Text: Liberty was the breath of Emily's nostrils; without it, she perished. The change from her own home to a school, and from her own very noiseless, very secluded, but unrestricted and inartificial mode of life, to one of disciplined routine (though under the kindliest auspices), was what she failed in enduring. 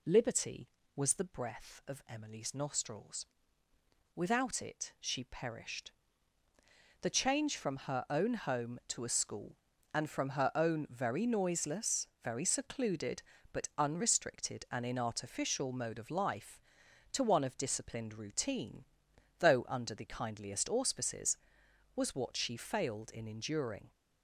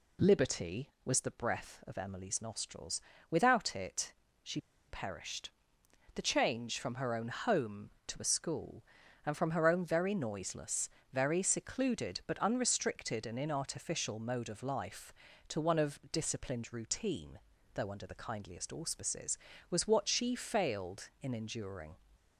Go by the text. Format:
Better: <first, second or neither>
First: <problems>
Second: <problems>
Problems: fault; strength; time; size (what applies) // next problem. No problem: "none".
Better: first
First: none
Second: pauses between "she" and "perished"; slight; at 4.5 s; 0.28 s long